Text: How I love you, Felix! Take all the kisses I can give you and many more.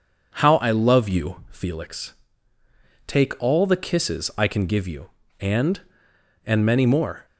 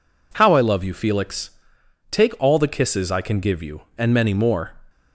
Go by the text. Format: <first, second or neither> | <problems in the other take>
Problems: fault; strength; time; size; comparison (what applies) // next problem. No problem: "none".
second | says "and" twice; at 6.4 s